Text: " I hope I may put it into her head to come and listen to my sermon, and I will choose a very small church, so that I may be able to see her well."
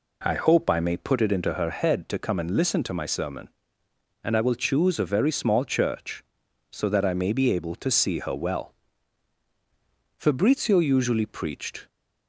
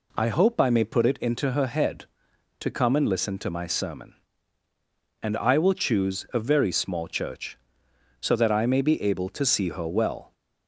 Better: second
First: goes on to say "Fabrizio usually preached"; strong; from 10.1 s on; 1.7 s long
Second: none

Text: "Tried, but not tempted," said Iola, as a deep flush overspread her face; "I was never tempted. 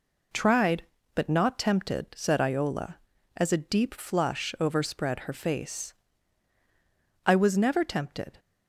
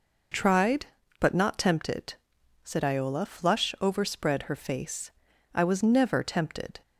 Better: first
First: none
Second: skips "as a deep"; at 3.2 s

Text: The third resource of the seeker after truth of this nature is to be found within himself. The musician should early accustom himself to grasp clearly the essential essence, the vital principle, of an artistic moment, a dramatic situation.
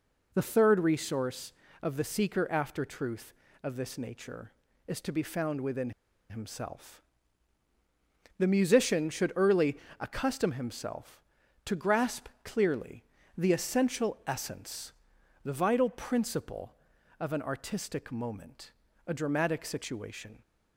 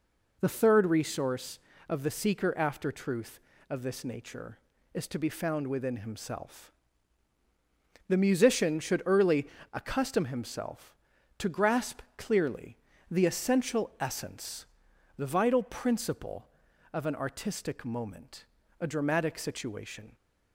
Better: second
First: pauses between "within" and "himself"; at 5.9 s; 0.38 s long // pauses between "early" and "accustom"; slight; at 9.7 s; 0.22 s long // pauses between "grasp" and "clearly"; slight; at 12.2 s; 0.16 s long // pauses between "clearly" and "the"; slight; at 13.0 s; 0.32 s long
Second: pauses between "early" and "accustom"; slight; at 9.4 s; 0.25 s long // pauses between "grasp" and "clearly"; slight; at 12.0 s; 0.16 s long // pauses between "clearly" and "the"; slight; at 12.7 s; 0.32 s long

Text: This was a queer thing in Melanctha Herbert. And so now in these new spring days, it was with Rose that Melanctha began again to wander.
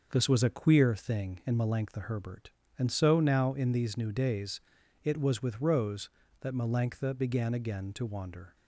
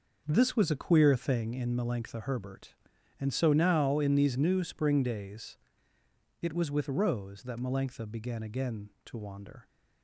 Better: second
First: starts louder than the rest; until 1.1 s; 6.5 dB // skips "spring"; at 4.1 s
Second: none

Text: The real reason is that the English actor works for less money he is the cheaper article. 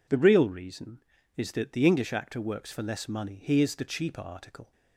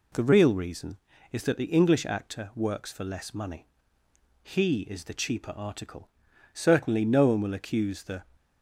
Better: first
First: none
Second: pauses between "money" and "he"; noticeable; at 3.6 s; 0.80 s long // goes on to say "Certainly no one will accuse the"; strong; from 6.5 s on; 1.7 s long

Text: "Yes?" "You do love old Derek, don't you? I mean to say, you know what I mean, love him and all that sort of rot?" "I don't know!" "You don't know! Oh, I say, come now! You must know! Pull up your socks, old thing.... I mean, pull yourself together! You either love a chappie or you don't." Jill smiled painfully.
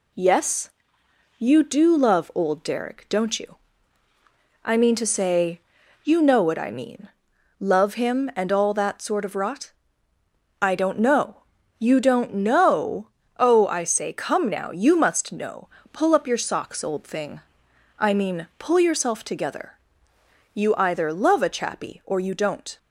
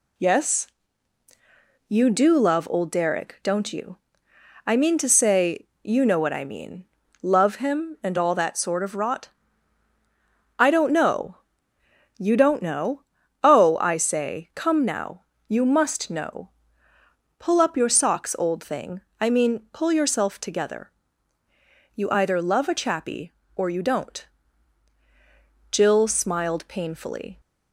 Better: second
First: stops before "Jill smiled painfully"; at 22.7 s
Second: none

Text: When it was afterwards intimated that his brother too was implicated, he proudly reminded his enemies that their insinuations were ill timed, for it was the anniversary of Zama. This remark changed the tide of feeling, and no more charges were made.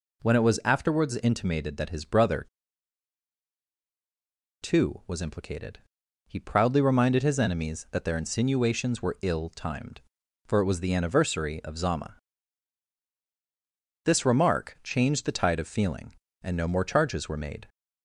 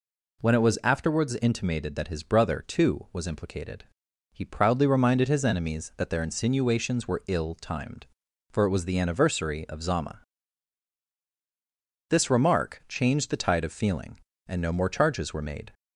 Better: second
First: pauses between "brother" and "too"; strong; at 2.4 s; 2.1 s long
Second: none

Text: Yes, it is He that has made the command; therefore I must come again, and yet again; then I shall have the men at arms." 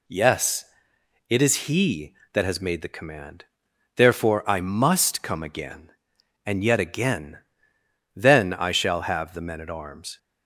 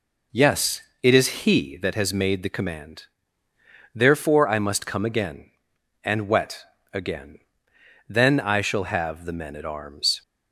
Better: first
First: none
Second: says "wet" for "yet"; at 6.2 s

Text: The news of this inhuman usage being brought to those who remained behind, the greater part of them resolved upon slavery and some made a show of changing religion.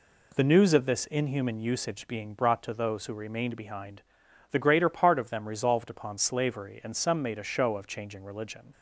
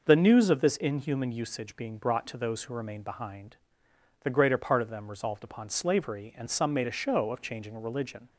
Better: neither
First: none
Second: none

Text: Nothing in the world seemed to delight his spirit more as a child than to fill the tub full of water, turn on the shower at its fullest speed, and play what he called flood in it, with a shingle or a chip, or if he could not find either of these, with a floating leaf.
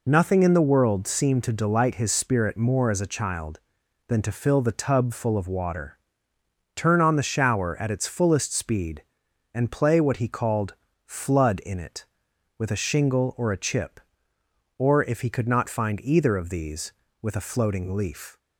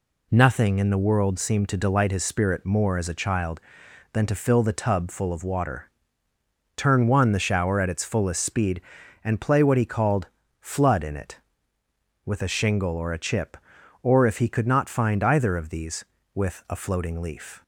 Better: first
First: pauses between "called" and "flood"; slight; at 10.7 s; 0.30 s long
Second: says "one" for "on"; at 7.0 s // pauses between "called" and "flood"; slight; at 10.2 s; 0.34 s long

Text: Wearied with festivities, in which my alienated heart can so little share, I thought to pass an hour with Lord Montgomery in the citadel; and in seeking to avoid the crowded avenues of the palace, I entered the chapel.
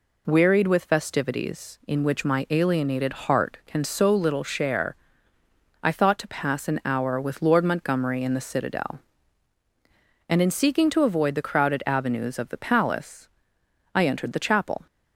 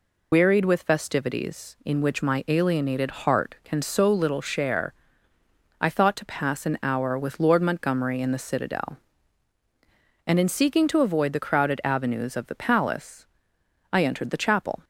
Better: first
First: none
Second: loses the start of "Wearied"; at 0.3 s; 85 ms

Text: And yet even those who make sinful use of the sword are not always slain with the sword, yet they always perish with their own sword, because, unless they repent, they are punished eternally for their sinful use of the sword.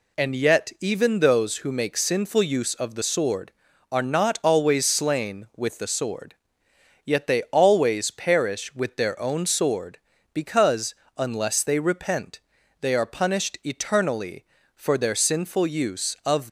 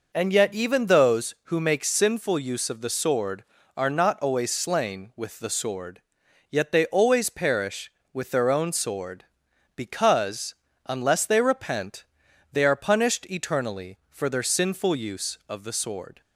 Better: second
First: stops before "the sword"; at 16.4 s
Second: none

